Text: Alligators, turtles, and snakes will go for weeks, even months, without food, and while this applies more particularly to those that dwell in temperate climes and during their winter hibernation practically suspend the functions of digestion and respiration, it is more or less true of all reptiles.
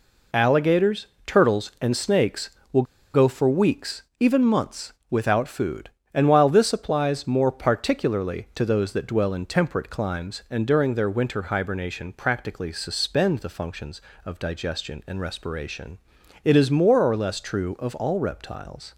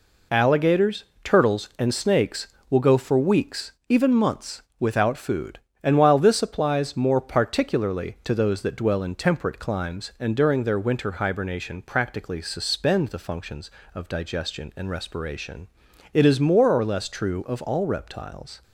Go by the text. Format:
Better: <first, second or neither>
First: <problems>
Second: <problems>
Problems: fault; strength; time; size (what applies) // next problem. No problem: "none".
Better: second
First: pauses between "will" and "go"; slight; at 2.8 s; 0.30 s long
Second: none